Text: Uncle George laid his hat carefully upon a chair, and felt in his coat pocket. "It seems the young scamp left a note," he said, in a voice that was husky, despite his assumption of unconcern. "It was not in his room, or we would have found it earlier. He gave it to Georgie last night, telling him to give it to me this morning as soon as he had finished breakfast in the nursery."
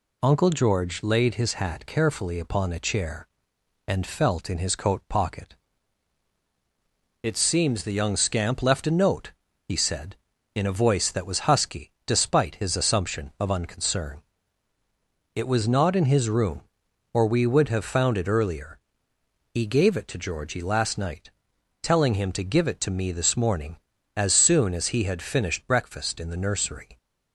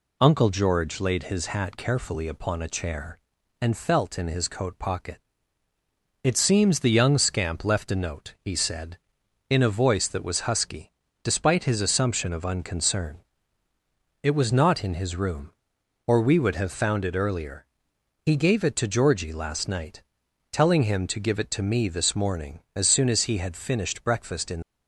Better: first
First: none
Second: stops before "the nursery"; at 24.6 s

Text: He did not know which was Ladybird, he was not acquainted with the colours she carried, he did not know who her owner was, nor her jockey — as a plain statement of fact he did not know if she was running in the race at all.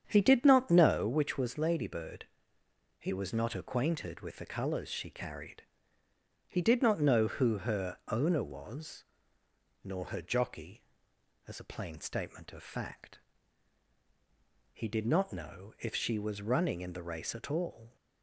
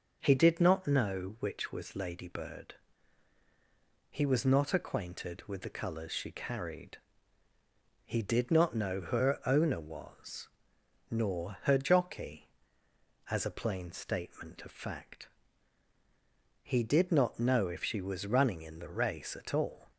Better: second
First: starts louder than the rest; strong; until 1.1 s; 8 dB // pauses between "fact" and "he"; strong; at 13.1 s; 1.5 s long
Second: pauses between "fact" and "he"; strong; at 15.2 s; 1.3 s long

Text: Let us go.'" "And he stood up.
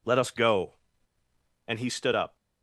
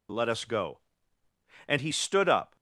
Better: neither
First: none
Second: none

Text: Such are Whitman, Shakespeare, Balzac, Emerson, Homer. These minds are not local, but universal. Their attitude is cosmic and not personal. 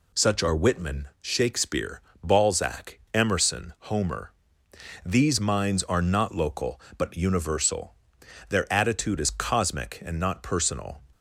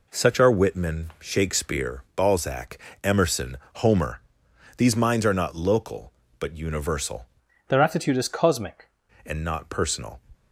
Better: first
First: none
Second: changes voice from "Their" to "cosmic"; from 7.6 to 8.8 s; 1.2 s long

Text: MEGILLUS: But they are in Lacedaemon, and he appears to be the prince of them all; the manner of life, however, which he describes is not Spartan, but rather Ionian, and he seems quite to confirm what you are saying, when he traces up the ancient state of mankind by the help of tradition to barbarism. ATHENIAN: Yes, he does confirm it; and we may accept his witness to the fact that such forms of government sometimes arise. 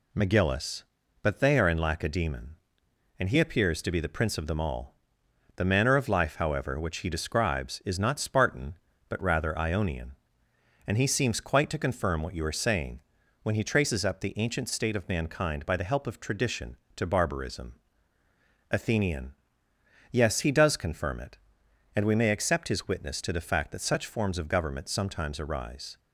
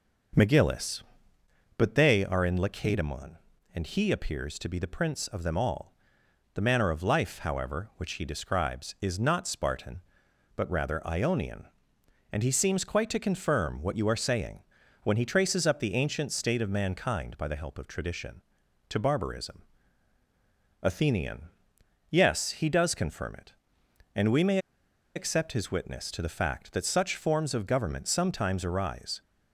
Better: first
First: none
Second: pauses between "may" and "accept"; noticeable; at 24.5 s; 0.57 s long

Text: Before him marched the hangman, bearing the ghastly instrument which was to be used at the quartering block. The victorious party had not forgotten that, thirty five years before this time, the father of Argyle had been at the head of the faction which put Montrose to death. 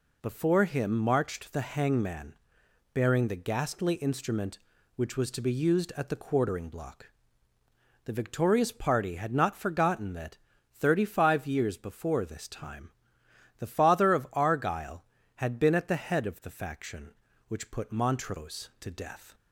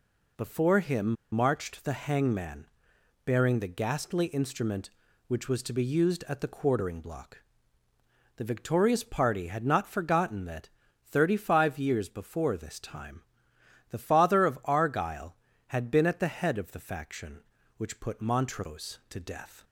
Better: first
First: none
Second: pauses between "him" and "marched"; slight; at 1.1 s; 0.19 s long

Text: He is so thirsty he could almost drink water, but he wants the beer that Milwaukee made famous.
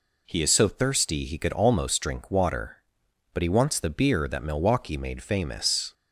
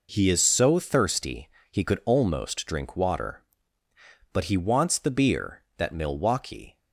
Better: first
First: none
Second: pauses between "thirsty" and "he"; slight; at 1.4 s; 0.22 s long // stops before "made famous"; at 6.7 s

